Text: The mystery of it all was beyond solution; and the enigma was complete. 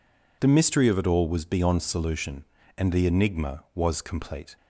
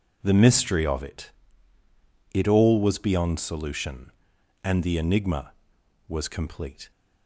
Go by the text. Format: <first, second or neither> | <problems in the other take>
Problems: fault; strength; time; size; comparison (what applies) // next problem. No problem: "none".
first | says "it" twice; at 2.3 s